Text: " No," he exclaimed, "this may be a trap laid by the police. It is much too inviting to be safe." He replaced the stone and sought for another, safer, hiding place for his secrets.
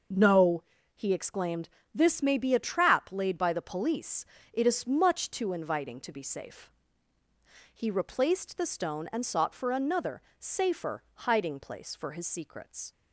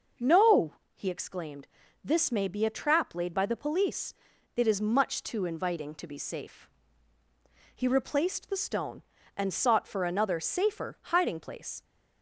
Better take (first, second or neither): first